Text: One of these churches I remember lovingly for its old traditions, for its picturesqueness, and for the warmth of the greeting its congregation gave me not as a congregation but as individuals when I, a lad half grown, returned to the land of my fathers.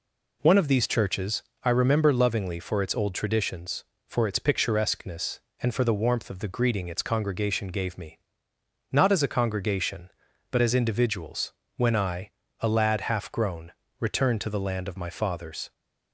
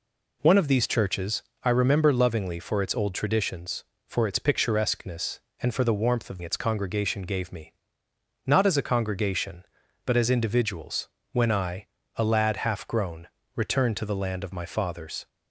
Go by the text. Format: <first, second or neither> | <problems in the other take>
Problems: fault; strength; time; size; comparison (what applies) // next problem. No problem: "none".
first | pauses between "churches" and "I"; slight; at 1.4 s; 0.22 s long; slight in the first // skips "the greeting"; at 6.4 s // pauses between "me" and "not"; noticeable; at 7.7 s; 0.70 s long; noticeable in the first // pauses between "individuals" and "when"; slight; at 11.0 s; 0.24 s long; slight in the first